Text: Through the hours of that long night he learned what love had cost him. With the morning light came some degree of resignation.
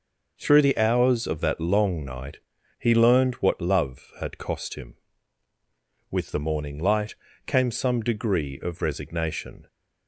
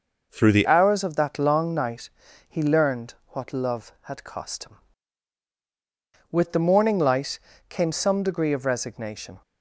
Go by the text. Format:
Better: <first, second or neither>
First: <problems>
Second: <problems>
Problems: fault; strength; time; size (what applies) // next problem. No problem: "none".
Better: first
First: pauses between "night" and "he"; at 2.3 s; 0.40 s long // pauses between "light" and "came"; slight; at 7.1 s; 0.32 s long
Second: changes voice at "hours"; from 0.6 s on; 8.8 s long // pauses between "night" and "he"; at 2.0 s; 0.38 s long // pauses between "learned" and "what"; slight; at 3.1 s; 0.16 s long // pauses between "light" and "came"; slight; at 7.3 s; 0.28 s long